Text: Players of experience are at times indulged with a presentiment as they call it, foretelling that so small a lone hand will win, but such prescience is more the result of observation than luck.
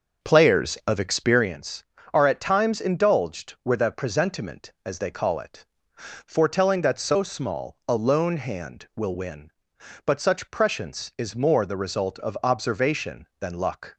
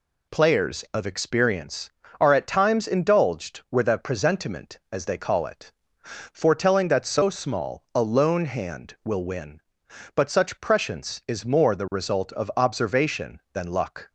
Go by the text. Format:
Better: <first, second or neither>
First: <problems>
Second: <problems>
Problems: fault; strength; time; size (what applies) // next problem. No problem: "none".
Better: second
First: starts louder than the rest; noticeable; until 1.4 s; 6 dB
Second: none